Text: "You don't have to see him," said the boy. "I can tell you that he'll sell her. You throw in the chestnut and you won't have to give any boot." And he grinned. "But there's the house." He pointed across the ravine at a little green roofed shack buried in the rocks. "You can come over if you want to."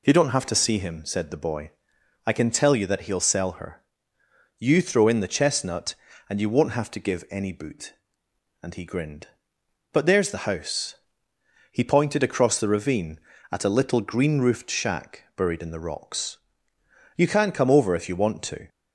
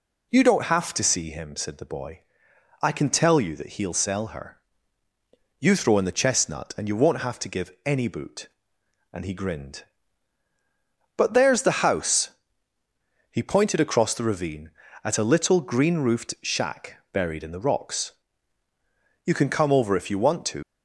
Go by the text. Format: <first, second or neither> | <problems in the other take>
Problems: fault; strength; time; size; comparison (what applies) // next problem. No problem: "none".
first | leaves "to" unfinished; at 20.6 s; 100 ms